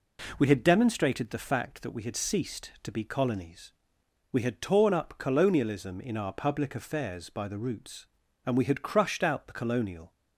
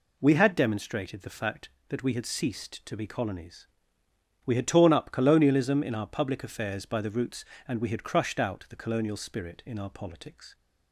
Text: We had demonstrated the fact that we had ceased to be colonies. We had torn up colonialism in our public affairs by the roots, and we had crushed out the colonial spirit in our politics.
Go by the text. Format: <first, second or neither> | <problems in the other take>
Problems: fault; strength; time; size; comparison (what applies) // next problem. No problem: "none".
second | stops before "spirit in our politics"; at 10.1 s